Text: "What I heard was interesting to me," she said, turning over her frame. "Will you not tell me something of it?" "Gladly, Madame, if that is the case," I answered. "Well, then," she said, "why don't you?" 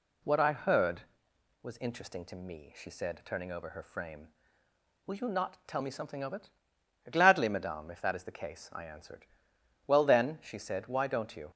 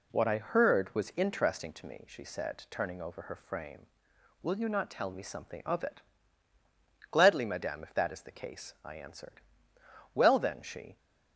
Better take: first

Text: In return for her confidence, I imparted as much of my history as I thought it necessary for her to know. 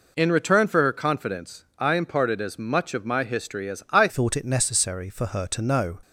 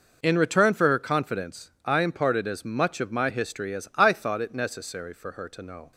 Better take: second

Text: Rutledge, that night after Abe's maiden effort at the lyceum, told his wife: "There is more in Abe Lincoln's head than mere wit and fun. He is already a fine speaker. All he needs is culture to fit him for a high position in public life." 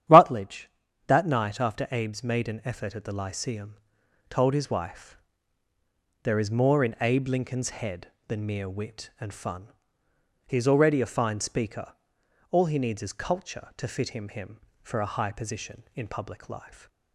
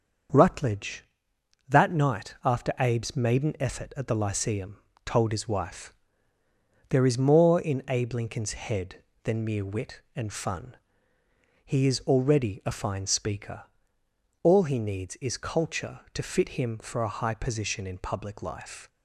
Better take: second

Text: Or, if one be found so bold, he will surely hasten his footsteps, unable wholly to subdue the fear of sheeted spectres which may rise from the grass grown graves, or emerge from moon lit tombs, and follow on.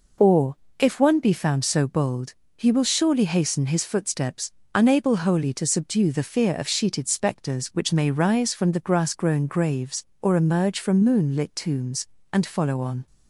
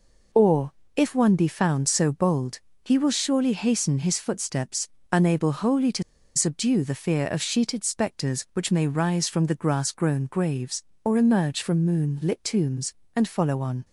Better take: first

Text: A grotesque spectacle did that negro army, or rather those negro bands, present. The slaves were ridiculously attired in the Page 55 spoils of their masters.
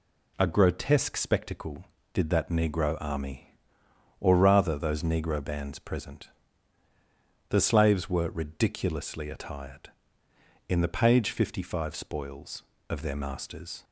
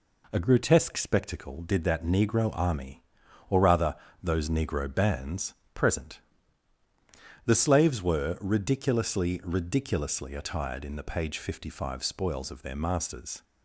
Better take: first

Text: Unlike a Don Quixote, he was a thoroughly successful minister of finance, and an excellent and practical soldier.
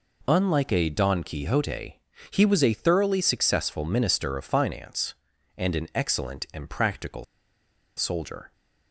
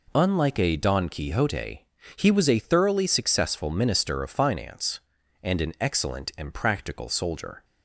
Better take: second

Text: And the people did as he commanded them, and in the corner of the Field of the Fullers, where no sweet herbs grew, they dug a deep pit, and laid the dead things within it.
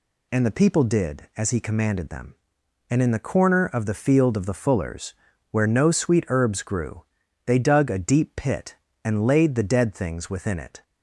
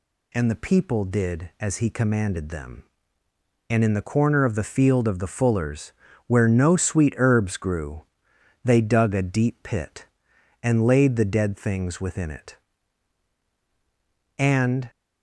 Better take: first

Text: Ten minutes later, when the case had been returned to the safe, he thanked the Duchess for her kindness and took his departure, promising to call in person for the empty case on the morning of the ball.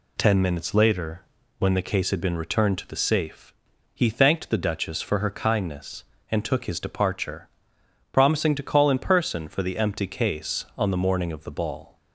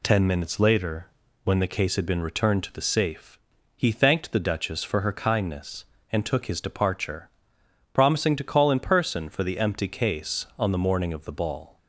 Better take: neither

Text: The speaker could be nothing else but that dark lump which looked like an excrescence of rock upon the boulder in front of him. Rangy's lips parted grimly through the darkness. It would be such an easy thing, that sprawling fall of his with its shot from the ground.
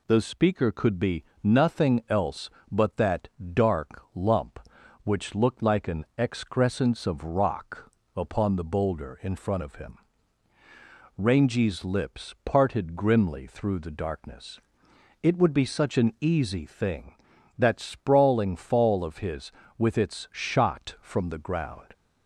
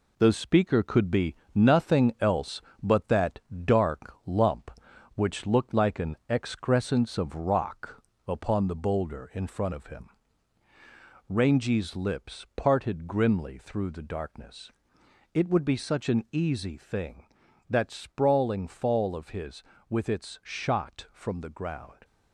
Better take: first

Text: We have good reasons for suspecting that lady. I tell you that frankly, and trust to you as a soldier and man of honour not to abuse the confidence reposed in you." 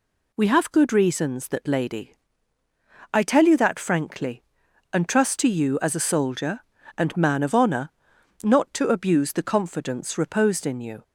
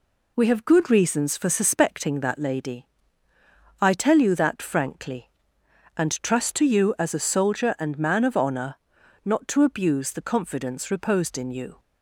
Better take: second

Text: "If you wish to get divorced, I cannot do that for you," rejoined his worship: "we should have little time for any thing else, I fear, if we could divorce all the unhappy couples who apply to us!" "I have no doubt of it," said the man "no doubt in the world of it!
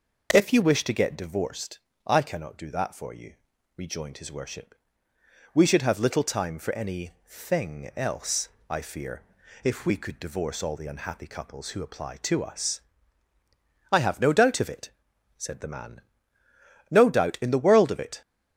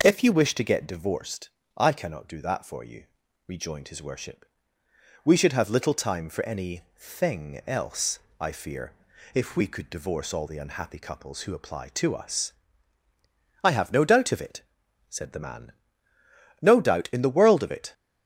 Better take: neither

